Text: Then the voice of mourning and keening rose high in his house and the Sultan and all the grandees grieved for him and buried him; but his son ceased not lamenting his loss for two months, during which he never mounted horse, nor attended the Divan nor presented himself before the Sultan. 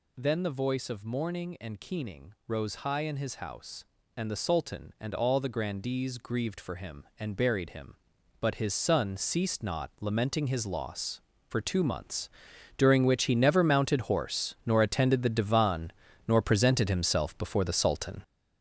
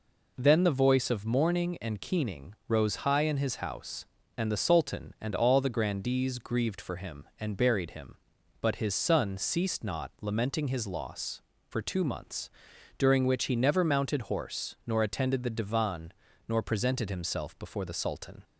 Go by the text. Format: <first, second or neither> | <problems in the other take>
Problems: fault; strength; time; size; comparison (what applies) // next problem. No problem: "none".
second | gets louder; strong; throughout; 8 dB // pauses between "Divan" and "nor"; slight; at 15.9 s; 0.36 s long; slight in the second